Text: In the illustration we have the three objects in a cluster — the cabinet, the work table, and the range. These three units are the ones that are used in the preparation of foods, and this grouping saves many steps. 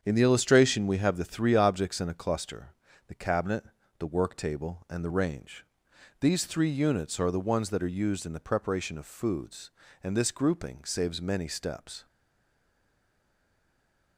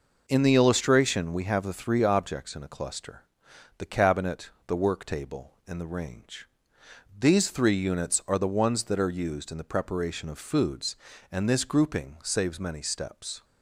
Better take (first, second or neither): second